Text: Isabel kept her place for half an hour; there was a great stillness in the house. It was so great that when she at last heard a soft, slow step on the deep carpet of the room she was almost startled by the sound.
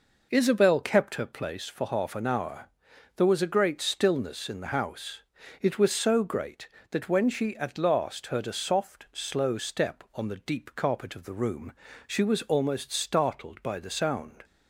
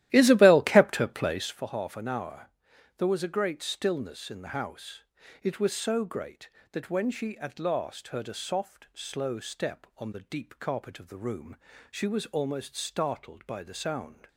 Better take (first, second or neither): first